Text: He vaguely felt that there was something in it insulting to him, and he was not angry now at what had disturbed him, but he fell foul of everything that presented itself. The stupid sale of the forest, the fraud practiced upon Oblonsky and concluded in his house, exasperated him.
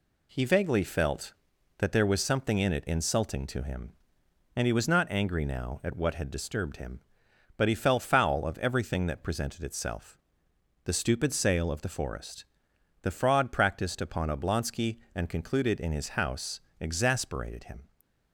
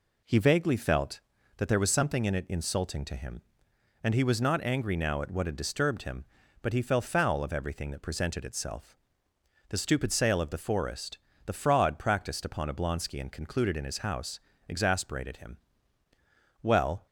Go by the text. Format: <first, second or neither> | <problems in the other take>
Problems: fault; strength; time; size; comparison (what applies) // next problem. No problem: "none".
first | goes on to say "Well"; slight; from 16.6 s on; 0.44 s long